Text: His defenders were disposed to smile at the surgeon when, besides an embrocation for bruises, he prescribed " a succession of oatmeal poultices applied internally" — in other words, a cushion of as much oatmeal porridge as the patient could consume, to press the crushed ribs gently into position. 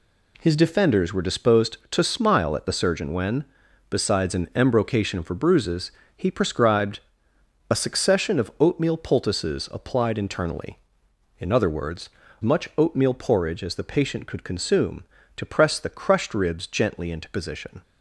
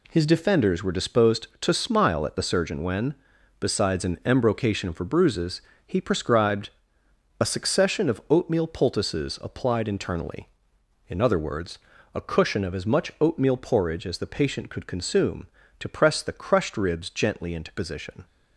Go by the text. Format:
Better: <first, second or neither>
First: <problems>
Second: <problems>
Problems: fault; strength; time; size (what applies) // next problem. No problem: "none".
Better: second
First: skips "a cushion of as"; at 12.2 s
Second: none